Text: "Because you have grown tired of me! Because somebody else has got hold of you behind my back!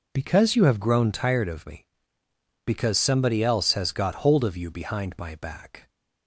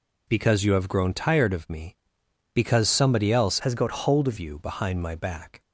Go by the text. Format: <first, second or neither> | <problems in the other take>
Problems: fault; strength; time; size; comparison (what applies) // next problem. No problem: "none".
first | changes voice from "has" to "of"; from 3.6 to 4.3 s; 0.7 s long